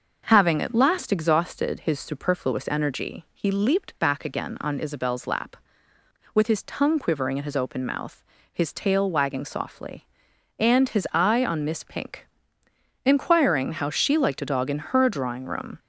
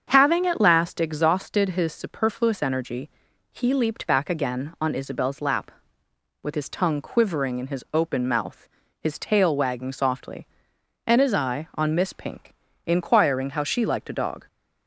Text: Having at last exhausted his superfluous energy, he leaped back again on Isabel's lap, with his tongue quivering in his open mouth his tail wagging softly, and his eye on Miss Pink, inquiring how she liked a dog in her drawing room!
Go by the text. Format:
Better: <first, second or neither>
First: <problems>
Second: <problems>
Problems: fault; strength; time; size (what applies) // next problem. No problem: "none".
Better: first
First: starts louder than the rest; until 1.2 s; 6 dB // pauses between "mouth" and "his"; slight; at 8.2 s; 0.28 s long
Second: starts louder than the rest; strong; until 1.0 s; 7 dB // pauses between "mouth" and "his"; slight; at 8.6 s; 0.32 s long // stops before "in her drawing room"; at 14.4 s